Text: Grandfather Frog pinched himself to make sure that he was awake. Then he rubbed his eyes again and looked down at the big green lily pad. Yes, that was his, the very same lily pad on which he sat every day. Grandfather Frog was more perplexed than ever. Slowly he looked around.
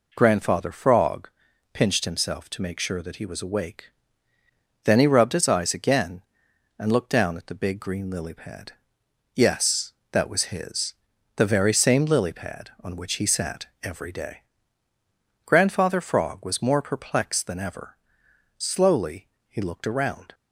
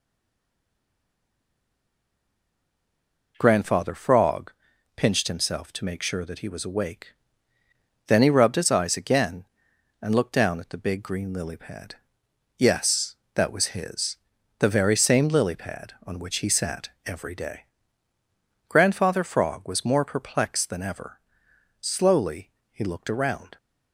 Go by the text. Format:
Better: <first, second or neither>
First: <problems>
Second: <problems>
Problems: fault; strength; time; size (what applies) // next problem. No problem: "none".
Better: first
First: pauses between "Frog" and "pinched"; at 1.2 s; 0.42 s long // pauses between "Slowly" and "he"; slight; at 19.2 s; 0.20 s long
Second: stays silent before the first word; strong; until 3.3 s; 3.3 s long // pauses between "Frog" and "pinched"; at 4.5 s; 0.42 s long // pauses between "Slowly" and "he"; slight; at 22.5 s; 0.20 s long